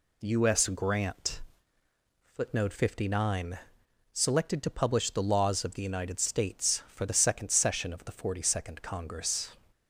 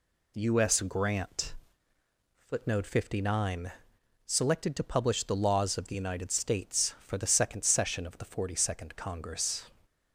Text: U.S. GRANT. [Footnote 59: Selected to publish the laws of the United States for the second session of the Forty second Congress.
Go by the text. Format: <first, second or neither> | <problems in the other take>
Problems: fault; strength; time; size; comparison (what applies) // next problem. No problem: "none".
neither | none